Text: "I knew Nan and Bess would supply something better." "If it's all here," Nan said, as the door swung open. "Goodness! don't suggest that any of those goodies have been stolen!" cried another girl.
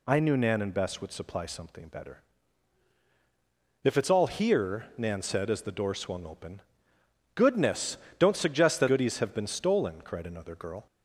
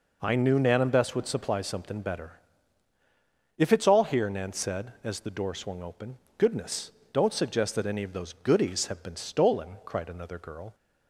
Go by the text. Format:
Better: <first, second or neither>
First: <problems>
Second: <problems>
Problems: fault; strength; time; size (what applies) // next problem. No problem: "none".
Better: second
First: skips "any of those"; at 8.8 s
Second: none